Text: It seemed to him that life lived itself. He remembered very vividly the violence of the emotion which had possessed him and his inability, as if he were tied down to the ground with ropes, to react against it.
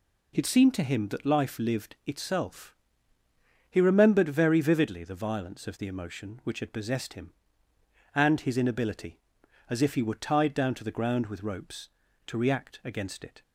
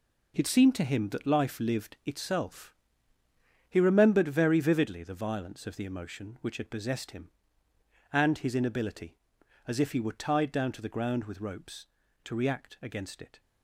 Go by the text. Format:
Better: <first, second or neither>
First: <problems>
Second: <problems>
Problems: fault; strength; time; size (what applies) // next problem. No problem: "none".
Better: first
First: none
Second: gets quieter; strong; throughout; 9 dB